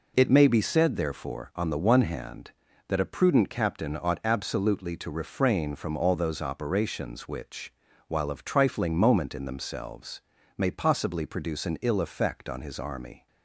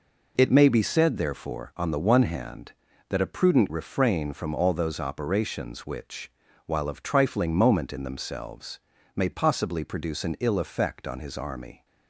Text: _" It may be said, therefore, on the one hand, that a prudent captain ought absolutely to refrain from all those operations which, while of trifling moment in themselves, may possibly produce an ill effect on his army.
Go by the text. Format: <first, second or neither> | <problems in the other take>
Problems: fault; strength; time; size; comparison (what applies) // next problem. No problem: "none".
first | skips "captain ought absolutely to"; at 3.6 s